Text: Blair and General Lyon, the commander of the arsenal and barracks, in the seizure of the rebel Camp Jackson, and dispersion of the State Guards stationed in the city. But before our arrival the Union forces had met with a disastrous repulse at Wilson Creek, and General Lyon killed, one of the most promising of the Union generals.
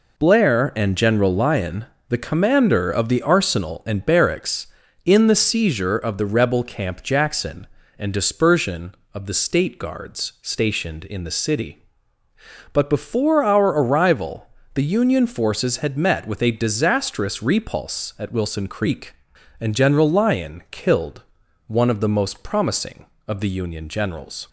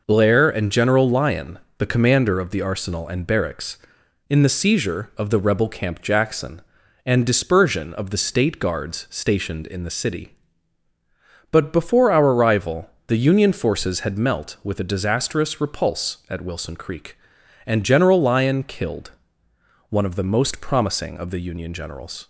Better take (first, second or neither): first